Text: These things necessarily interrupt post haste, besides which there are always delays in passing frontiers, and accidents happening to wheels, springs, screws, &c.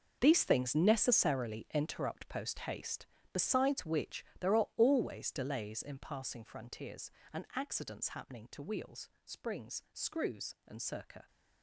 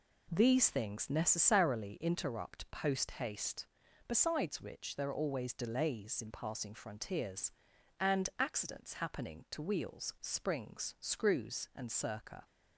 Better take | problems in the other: second | gets quieter; strong; throughout; 13 dB

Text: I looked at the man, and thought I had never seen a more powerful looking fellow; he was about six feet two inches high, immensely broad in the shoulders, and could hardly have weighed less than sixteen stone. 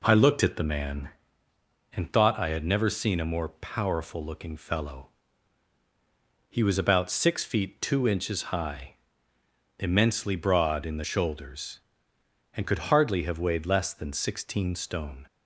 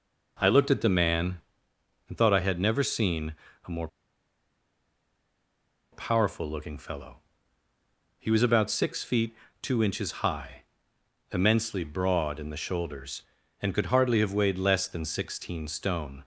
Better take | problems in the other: first | pauses between "seen" and "a"; slight; at 3.3 s; 0.32 s long // pauses between "more" and "powerful"; strong; at 3.8 s; 2.0 s long // pauses between "feet" and "two"; slight; at 9.3 s; 0.26 s long

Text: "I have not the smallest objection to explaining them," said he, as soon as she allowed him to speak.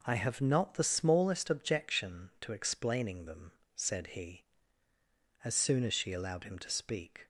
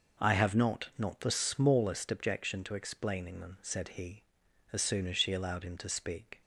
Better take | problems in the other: first | says "not" twice; at 0.9 s

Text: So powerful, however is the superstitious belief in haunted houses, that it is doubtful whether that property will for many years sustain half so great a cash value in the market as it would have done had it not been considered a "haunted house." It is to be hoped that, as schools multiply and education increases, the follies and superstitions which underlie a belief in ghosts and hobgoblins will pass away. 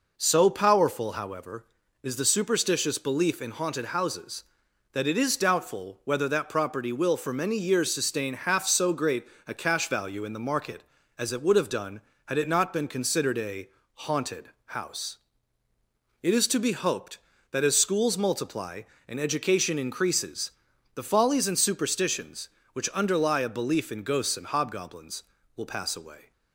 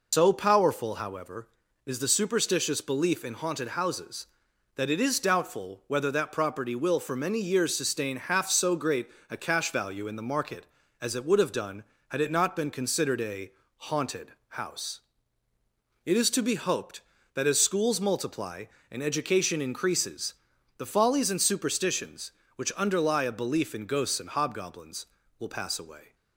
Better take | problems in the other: first | loses the start of "So"; at 0.1 s; 120 ms // pauses between "great" and "a"; slight; at 9.0 s; 0.22 s long; slight in the first // pauses between "a" and "haunted"; slight; at 13.5 s; 0.24 s long; slight in the first // pauses between "haunted" and "house"; slight; at 14.3 s; 0.16 s long; slight in the first

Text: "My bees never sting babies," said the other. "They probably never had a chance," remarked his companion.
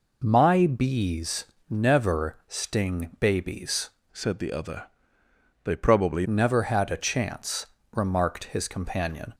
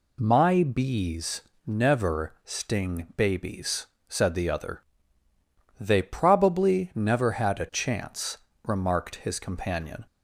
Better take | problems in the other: second | pauses between "bees" and "never"; slight; at 1.4 s; 0.22 s long; slight in the second // changes voice from "said" to "probably"; from 4.1 to 6.2 s; 2.1 s long

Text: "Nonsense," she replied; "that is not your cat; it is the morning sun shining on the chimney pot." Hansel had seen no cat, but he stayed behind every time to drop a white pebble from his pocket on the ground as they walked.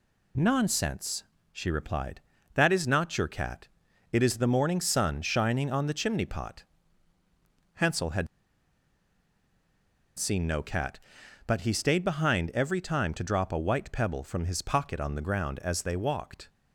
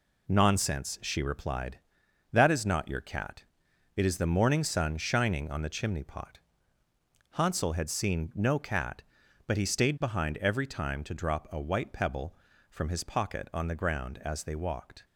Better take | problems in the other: second | pauses between "had" and "seen"; strong; at 8.2 s; 1.9 s long

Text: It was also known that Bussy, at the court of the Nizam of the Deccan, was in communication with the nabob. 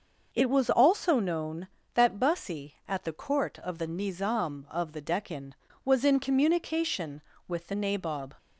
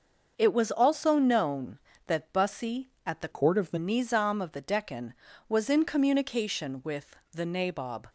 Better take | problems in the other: first | starts louder than the rest; until 1.3 s; 6 dB; noticeable in the first // changes voice from "court" to "the"; from 3.3 to 3.7 s; 0.4 s long // pauses between "with" and "the"; slight; at 7.1 s; 0.16 s long

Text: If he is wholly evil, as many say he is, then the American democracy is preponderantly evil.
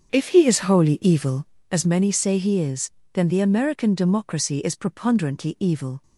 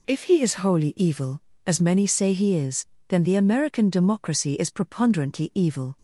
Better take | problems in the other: second | starts louder than the rest; strong; until 1.6 s; 7.5 dB

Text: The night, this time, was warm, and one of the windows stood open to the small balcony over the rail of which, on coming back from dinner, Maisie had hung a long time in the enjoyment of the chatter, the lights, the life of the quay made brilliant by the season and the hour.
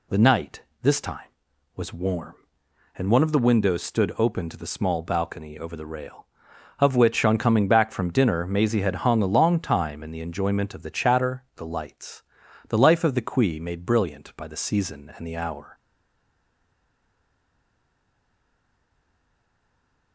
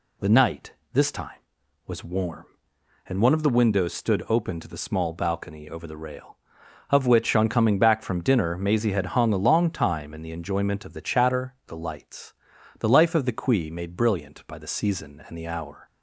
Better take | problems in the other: second | stays silent after the last word; strong; from 15.7 s on; 4.4 s long

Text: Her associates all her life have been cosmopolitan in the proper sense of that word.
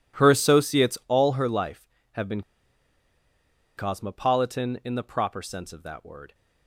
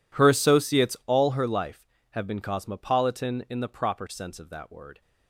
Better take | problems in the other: second | pauses between "been" and "cosmopolitan"; strong; at 2.4 s; 1.3 s long

